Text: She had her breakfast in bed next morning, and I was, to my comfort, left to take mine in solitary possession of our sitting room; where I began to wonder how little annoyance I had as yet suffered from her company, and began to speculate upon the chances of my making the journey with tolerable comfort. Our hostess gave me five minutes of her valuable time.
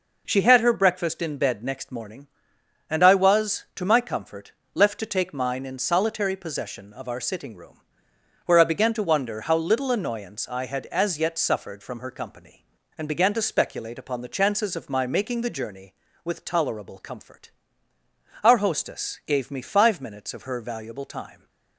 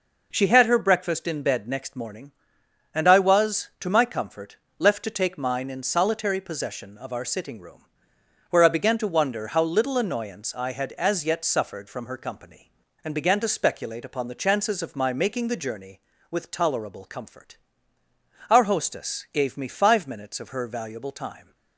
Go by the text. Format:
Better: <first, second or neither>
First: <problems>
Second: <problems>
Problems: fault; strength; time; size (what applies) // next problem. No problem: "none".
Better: neither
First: none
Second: none